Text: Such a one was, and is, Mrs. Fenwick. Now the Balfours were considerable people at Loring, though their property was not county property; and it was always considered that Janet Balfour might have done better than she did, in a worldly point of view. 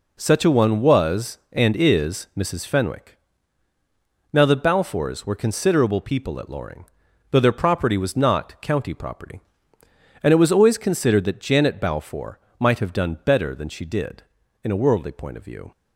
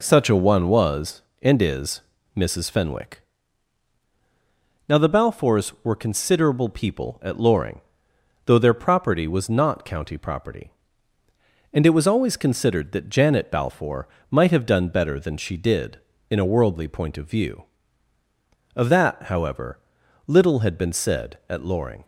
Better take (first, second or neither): first